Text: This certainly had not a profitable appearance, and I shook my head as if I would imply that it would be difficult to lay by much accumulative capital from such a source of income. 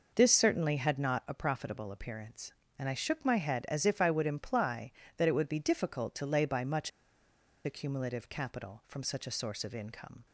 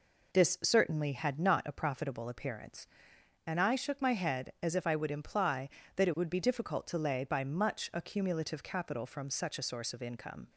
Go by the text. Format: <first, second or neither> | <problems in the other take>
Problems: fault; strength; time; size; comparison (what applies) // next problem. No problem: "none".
second | pauses between "much" and "accumulative"; noticeable; at 6.9 s; 0.75 s long